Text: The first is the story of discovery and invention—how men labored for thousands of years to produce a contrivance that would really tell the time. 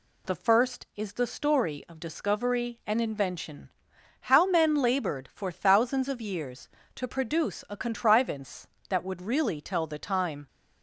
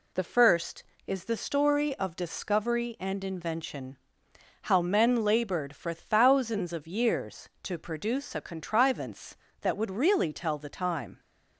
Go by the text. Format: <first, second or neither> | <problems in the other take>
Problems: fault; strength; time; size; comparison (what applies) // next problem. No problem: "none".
neither | none